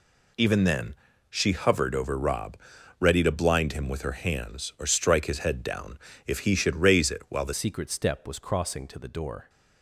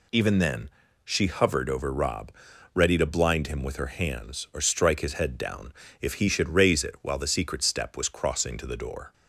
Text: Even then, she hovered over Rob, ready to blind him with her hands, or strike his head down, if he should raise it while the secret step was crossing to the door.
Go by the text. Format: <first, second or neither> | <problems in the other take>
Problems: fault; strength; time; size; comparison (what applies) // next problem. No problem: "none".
second | changes voice at "secret"; from 7.5 s on; 1.9 s long